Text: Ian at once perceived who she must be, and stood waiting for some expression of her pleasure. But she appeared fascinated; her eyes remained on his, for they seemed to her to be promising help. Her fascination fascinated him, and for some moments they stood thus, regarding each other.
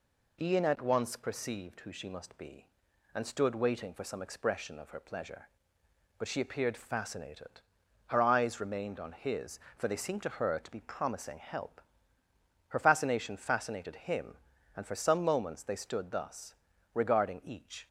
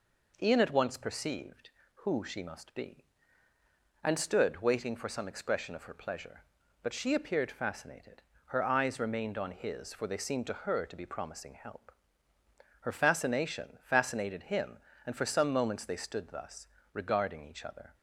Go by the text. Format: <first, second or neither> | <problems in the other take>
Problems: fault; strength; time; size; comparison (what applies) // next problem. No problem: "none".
second | stops before "other"; at 17.8 s